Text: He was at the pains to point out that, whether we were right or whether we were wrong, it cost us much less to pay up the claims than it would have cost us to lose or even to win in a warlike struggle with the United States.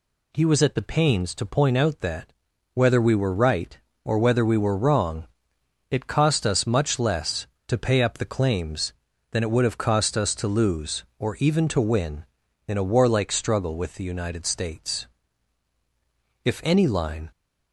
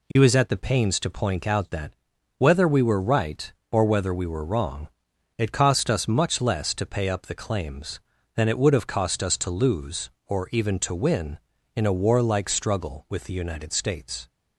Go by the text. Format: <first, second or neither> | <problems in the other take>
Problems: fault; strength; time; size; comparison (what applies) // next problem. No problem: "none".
second | goes on to say "If any line"; noticeable; from 16.4 s on; 0.88 s long